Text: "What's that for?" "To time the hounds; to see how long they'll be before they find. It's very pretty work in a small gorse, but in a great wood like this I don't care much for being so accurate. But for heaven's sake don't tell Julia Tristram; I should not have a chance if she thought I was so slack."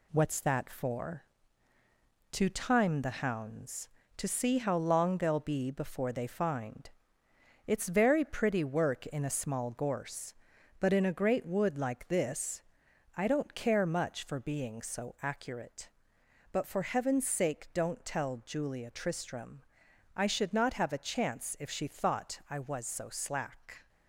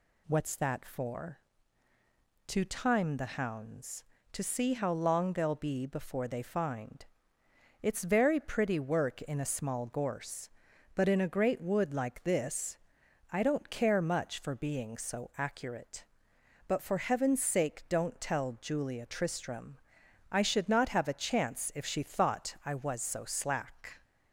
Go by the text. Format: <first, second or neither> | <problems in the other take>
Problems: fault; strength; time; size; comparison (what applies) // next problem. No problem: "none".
second | gets quieter; noticeable; throughout; 4 dB // pauses between "this" and "I"; noticeable; at 12.6 s; 0.56 s long; noticeable in the second